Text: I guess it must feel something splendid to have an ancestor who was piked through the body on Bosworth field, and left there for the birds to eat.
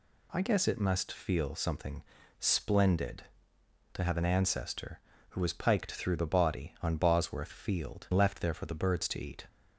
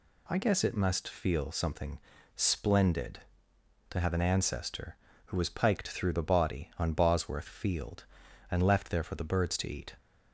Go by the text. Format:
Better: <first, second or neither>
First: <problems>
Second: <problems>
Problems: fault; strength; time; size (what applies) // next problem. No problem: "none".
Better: second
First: pauses between "something" and "splendid"; slight; at 2.0 s; 0.36 s long // skips "and"; at 8.1 s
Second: pauses between "something" and "splendid"; slight; at 1.9 s; 0.36 s long